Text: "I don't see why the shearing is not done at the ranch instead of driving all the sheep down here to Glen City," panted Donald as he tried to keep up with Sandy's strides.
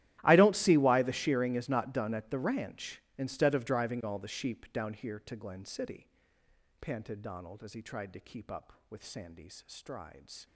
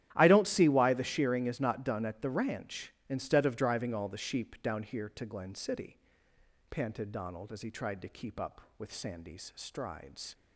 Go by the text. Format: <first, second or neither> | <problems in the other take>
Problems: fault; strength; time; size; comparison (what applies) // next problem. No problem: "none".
second | gets quieter; strong; throughout; 22 dB // starts louder than the rest; strong; until 1.2 s; 13 dB; strong in the second